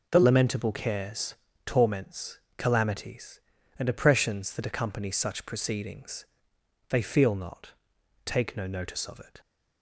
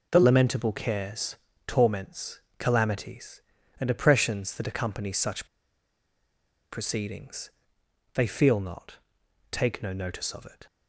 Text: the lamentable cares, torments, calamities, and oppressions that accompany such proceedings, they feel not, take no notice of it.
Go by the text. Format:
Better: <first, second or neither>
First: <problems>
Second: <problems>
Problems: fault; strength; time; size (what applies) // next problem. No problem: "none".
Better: first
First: none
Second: pauses between "such" and "proceedings"; strong; at 5.4 s; 1.2 s long